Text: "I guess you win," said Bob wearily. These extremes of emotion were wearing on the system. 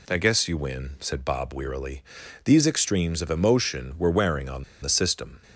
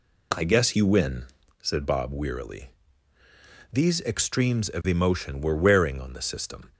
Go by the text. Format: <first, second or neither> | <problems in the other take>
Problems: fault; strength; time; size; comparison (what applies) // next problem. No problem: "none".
second | pauses between "on" and "the"; slight; at 4.6 s; 0.17 s long